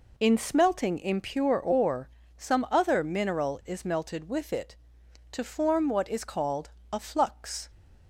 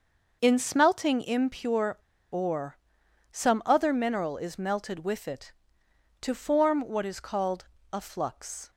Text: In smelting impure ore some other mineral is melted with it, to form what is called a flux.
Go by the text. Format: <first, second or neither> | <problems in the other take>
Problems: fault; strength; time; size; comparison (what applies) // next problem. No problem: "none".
first | starts louder than the rest; noticeable; until 1.4 s; 6 dB // pauses between "impure" and "ore"; slight; at 1.9 s; 0.35 s long // pauses between "ore" and "some"; noticeable; at 2.7 s; 0.56 s long; slight in the first // pauses between "called" and "a"; slight; at 7.6 s; 0.26 s long; slight in the first